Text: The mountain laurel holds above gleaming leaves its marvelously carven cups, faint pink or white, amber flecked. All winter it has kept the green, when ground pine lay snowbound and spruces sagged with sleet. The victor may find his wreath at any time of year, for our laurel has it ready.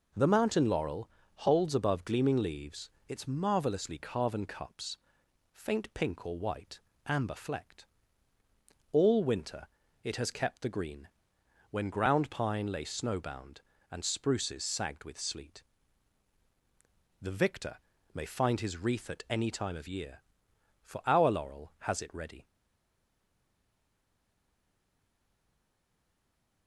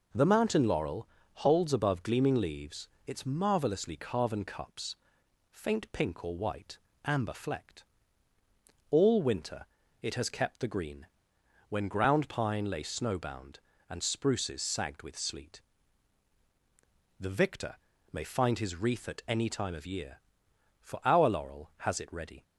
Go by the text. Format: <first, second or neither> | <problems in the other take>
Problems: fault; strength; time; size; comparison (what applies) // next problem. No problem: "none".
second | pauses between "laurel" and "holds"; slight; at 1.0 s; 0.28 s long; slight in the second // pauses between "leaves" and "its"; slight; at 2.9 s; 0.18 s long; slight in the second // pauses between "winter" and "it"; slight; at 9.6 s; 0.34 s long; slight in the second // pauses between "victor" and "may"; slight; at 17.7 s; 0.34 s long; slight in the second // stays silent after the last word; strong; from 22.4 s on; 4.2 s long